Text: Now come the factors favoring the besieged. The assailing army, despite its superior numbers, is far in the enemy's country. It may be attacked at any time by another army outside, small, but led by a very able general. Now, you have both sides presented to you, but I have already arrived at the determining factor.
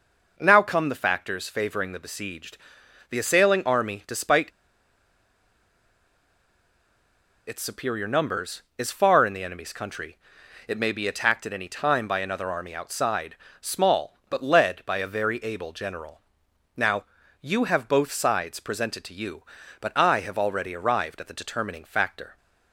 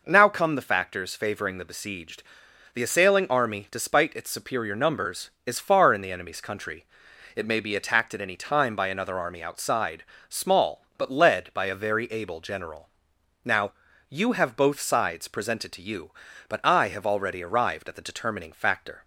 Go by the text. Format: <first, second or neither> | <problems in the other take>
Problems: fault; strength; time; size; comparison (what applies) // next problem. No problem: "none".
second | pauses between "despite" and "its"; strong; at 4.5 s; 2.9 s long